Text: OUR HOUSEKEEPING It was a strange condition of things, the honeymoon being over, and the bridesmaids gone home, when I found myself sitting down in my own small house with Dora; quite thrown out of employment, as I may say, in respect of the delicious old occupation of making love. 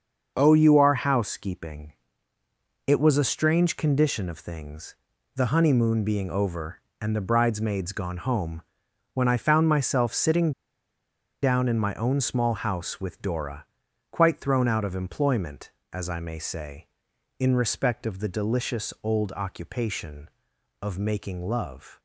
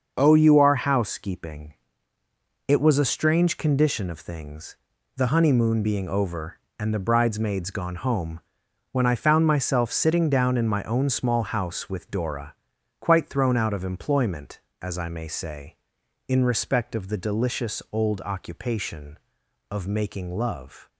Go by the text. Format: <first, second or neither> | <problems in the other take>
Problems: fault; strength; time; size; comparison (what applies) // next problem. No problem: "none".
second | starts louder than the rest; until 1.3 s; 6.5 dB; also in the second // pauses between "HOUSEKEEPING" and "It"; noticeable; at 1.9 s; 0.92 s long; noticeable in the second // pauses between "sitting" and "down"; noticeable; at 10.5 s; 0.90 s long